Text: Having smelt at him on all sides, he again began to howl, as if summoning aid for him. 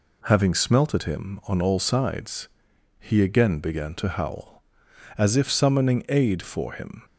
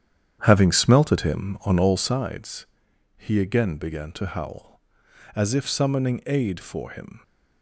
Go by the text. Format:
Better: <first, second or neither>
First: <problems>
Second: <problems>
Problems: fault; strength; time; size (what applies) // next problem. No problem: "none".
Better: first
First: none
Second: starts louder than the rest; strong; until 2.2 s; 9 dB